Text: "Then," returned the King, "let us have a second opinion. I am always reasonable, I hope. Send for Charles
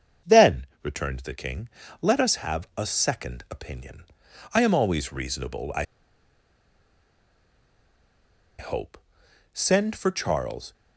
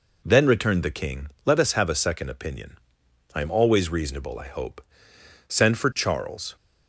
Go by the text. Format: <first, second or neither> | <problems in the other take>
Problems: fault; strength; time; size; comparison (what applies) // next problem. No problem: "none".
second | starts louder than the rest; until 1.4 s; 7 dB // pauses between "I" and "hope"; strong; at 5.8 s; 2.7 s long